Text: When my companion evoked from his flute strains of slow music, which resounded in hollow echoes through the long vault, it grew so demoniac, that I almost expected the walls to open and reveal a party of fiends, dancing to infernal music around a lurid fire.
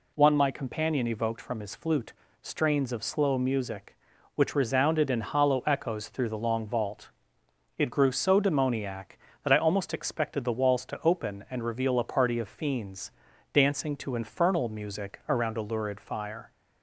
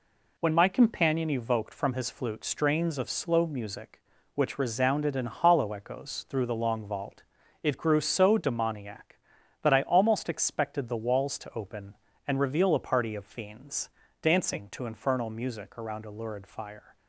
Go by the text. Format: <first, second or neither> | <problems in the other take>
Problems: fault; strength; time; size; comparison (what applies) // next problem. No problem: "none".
second | says "One" for "When"; at 0.1 s // pauses between "flute" and "strains"; slight; at 2.1 s; 0.30 s long